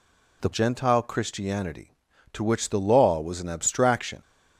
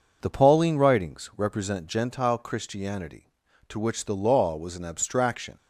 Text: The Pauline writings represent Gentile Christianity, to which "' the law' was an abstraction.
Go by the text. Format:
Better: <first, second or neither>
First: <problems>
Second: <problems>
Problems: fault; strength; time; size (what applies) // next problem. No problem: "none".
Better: second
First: skips "Pauline writings represent"; at 0.5 s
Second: none